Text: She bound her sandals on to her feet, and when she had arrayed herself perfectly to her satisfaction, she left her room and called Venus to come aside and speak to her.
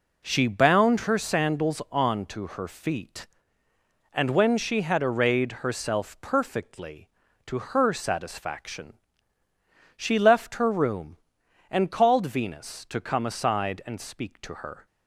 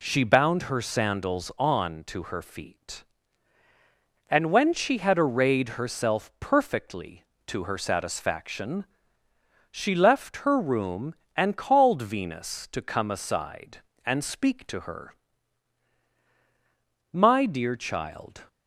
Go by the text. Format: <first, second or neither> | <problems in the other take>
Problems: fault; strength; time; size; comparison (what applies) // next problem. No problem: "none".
first | goes on to say "My dear child"; from 17.1 s on; 1.3 s long